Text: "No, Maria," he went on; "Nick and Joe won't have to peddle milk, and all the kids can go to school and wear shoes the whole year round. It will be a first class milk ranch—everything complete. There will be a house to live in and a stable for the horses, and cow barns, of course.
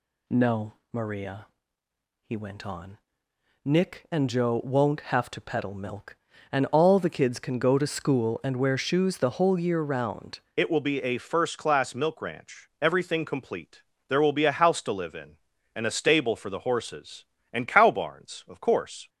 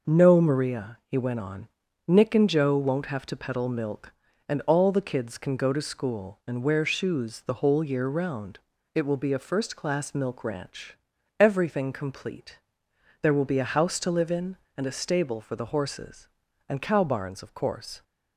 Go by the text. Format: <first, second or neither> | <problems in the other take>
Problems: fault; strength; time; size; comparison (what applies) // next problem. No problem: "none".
second | changes voice at "It"; from 10.5 s on; 8.5 s long